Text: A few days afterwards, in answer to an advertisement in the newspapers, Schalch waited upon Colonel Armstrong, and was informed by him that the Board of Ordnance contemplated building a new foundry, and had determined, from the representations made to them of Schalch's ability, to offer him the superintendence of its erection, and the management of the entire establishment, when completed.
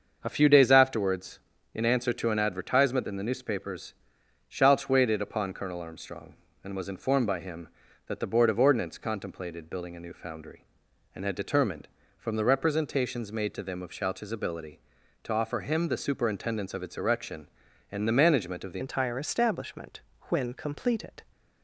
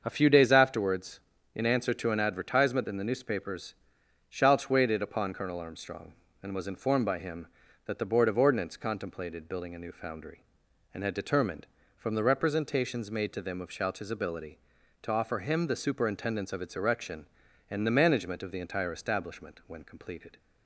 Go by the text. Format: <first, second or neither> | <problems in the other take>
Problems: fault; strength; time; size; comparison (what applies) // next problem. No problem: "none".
second | starts louder than the rest; until 1.2 s; 6.5 dB; also in the second // changes voice at "entire"; from 18.7 s on; 2.5 s long